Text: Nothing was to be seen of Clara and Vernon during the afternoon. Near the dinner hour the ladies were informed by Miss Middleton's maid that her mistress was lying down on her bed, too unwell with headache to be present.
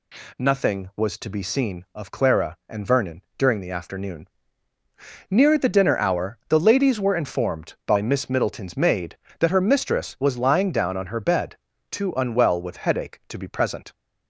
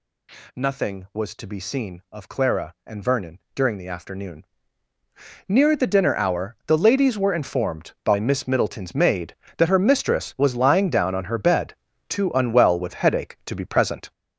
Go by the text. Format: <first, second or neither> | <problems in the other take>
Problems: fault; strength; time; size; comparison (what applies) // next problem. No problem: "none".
first | gets louder; strong; throughout; 7.5 dB // pauses between "Vernon" and "during"; slight; at 3.3 s; 0.16 s long; slight in the first